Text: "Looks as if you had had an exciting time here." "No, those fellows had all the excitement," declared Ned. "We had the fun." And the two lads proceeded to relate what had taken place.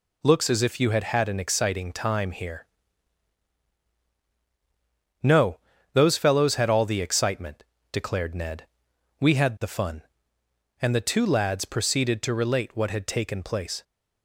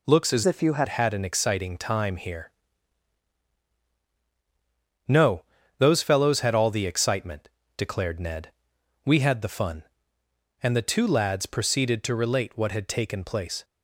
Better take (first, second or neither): first